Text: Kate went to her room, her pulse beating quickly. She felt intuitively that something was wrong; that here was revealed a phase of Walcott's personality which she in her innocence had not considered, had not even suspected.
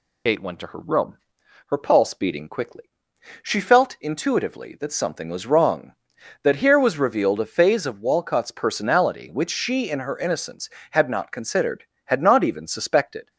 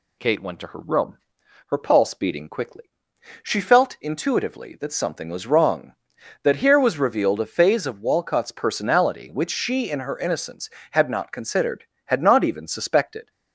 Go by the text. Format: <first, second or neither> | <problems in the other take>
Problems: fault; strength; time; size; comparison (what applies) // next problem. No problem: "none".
second | loses the start of "Kate"; at 0.2 s; 55 ms